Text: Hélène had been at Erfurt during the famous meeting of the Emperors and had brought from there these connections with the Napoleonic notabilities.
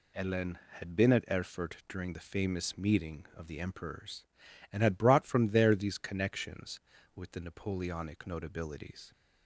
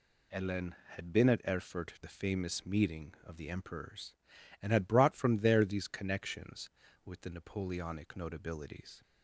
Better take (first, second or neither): first